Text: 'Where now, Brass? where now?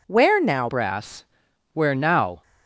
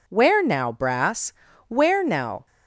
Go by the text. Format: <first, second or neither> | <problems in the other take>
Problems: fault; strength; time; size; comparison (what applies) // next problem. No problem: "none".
second | changes voice at "Brass"; from 0.6 s on; 1.8 s long